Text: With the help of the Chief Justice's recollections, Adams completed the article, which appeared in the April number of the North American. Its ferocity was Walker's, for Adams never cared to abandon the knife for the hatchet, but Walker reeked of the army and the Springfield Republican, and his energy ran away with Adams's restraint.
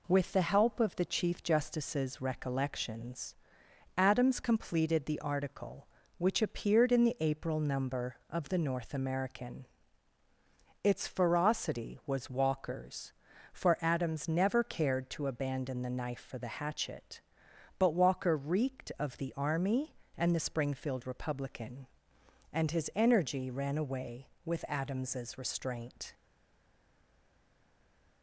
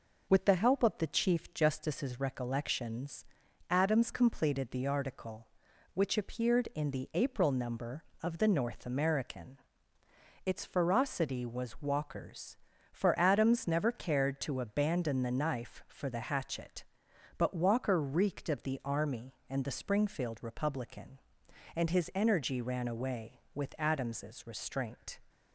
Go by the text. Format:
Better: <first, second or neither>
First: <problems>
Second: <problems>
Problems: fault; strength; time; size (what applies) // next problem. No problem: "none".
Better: second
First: stays silent after the last word; noticeable; from 26.1 s on; 2.1 s long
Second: none